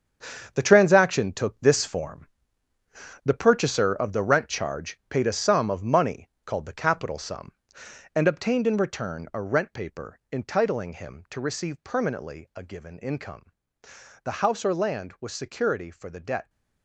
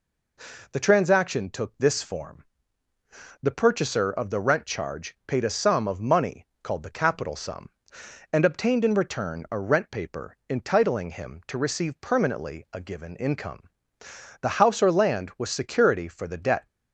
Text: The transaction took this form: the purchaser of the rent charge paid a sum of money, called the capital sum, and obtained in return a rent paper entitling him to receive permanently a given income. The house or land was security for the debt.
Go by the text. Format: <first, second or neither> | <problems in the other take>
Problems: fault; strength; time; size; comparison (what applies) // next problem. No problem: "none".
second | gets quieter; strong; throughout; 10.5 dB